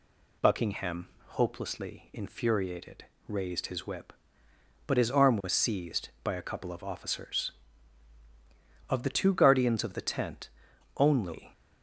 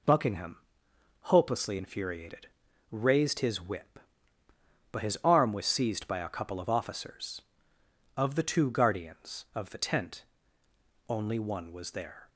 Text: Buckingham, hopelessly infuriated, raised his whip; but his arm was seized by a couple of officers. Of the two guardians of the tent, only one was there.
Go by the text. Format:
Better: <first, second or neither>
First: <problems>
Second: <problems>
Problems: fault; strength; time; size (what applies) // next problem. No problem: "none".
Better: second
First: stops before "one was there"; at 11.5 s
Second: none